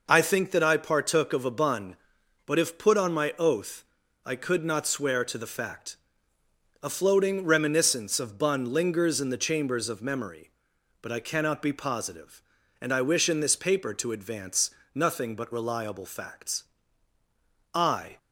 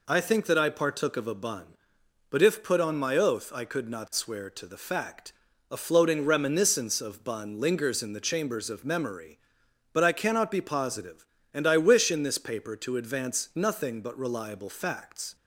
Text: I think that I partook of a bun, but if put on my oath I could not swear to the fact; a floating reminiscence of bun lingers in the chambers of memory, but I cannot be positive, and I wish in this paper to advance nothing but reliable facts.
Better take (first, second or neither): second